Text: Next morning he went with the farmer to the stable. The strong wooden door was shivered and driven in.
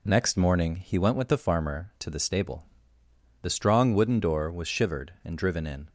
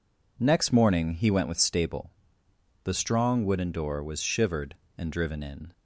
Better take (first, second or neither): first